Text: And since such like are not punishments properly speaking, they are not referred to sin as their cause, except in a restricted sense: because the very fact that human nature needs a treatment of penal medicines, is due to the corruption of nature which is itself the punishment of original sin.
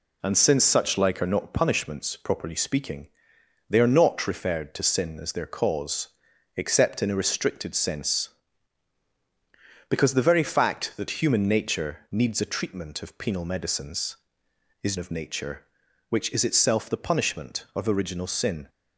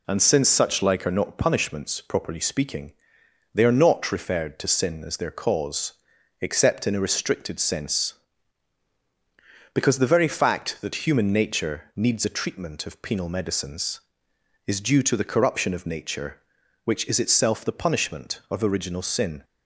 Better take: second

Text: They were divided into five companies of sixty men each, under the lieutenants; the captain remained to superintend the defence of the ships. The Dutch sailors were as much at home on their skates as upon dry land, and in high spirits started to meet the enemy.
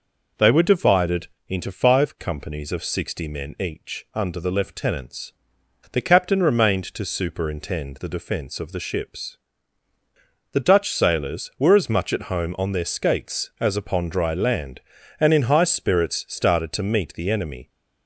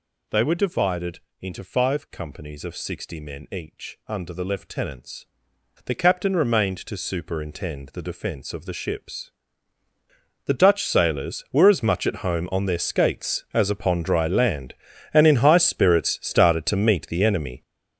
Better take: first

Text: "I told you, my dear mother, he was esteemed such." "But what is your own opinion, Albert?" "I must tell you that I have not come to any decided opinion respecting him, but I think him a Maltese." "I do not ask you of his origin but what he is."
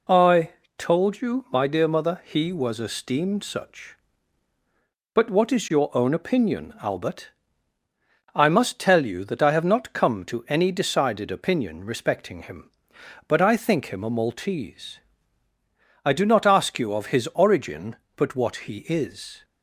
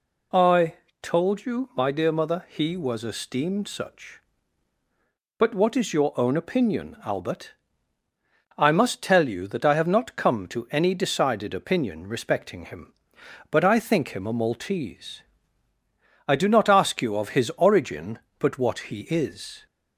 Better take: second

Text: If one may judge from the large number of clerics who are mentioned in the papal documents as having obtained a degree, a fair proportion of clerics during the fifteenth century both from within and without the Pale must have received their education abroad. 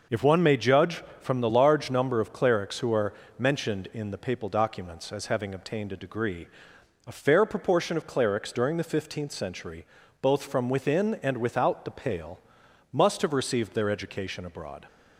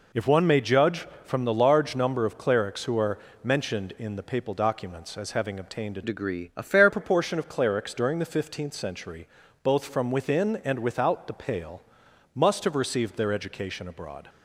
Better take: first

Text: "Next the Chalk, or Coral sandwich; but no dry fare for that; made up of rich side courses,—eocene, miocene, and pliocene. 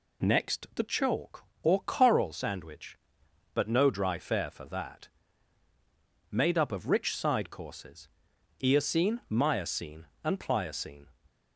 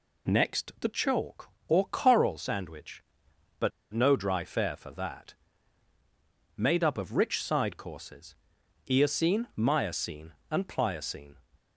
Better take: first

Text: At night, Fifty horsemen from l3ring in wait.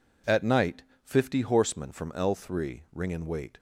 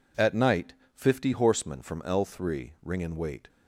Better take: neither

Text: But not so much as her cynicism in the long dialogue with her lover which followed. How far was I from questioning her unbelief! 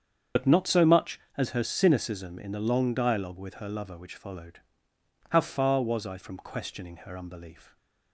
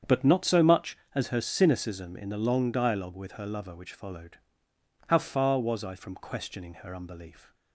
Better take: second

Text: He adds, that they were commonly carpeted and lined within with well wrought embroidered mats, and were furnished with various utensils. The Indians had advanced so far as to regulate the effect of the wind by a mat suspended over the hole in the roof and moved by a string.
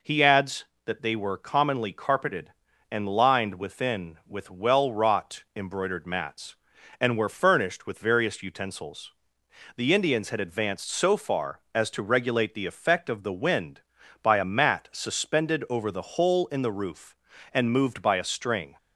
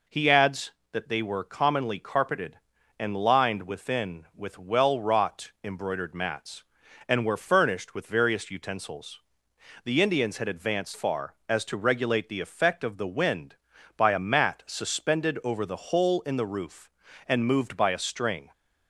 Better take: first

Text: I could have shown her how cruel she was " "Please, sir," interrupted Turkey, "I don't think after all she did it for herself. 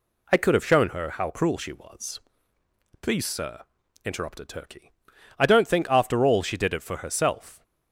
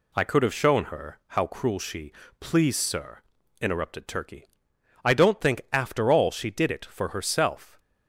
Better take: first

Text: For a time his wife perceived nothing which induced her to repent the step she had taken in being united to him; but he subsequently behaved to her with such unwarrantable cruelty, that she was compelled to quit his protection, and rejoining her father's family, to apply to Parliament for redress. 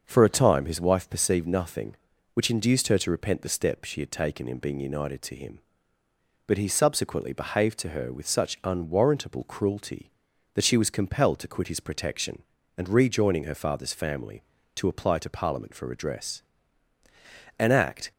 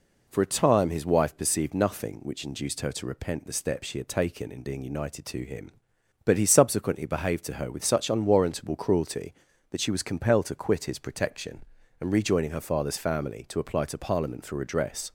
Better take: second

